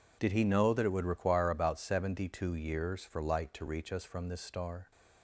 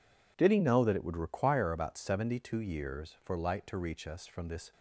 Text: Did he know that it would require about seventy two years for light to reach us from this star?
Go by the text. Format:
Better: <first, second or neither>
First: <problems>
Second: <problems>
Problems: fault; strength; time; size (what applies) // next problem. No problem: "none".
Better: first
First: none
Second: stops before "star"; at 4.7 s